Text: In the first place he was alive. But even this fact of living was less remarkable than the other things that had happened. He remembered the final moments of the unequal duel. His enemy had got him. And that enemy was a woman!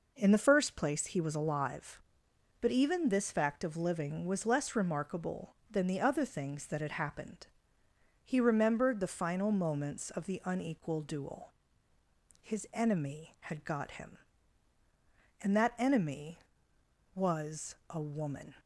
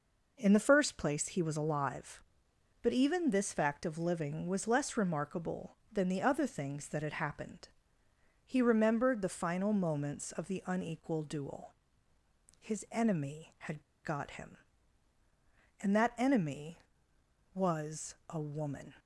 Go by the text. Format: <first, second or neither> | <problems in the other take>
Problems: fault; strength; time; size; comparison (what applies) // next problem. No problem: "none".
first | pauses between "had" and "got"; slight; at 13.8 s; 0.22 s long